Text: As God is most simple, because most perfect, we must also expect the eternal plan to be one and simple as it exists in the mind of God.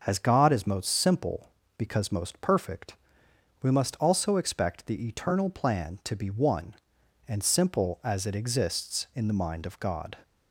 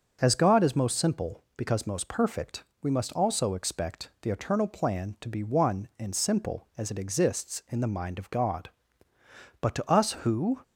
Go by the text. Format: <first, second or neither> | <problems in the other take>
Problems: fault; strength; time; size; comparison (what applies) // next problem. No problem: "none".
first | goes on to say "But to us who"; noticeable; from 9.6 s on; 0.98 s long